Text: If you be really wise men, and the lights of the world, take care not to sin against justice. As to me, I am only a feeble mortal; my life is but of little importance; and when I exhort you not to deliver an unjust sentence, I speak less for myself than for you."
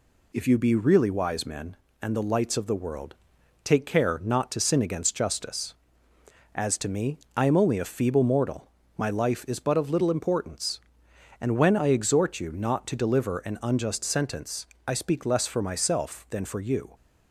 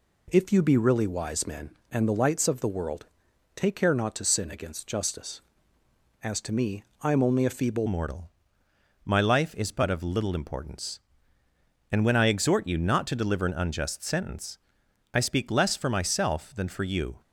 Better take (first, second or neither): first